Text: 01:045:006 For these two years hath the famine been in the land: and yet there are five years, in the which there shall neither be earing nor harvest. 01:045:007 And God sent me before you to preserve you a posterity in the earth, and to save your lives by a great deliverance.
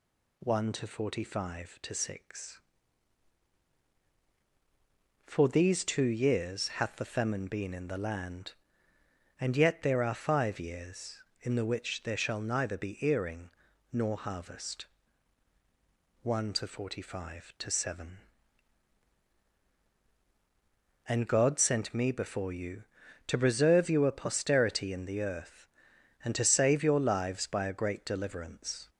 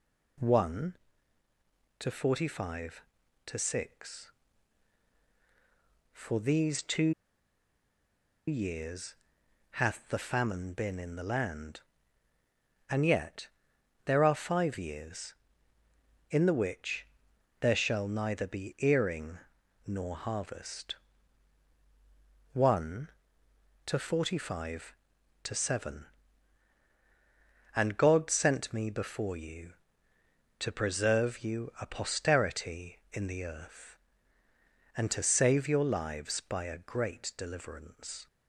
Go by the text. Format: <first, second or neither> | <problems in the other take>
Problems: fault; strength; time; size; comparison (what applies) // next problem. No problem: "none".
first | pauses between "two" and "years"; strong; at 7.1 s; 1.3 s long // pauses between "years" and "hath"; noticeable; at 9.1 s; 0.56 s long // pauses between "yet" and "there"; noticeable; at 13.4 s; 0.58 s long // pauses between "which" and "there"; noticeable; at 17.0 s; 0.54 s long // pauses between "earing" and "nor"; noticeable; at 19.3 s; 0.48 s long; also in the first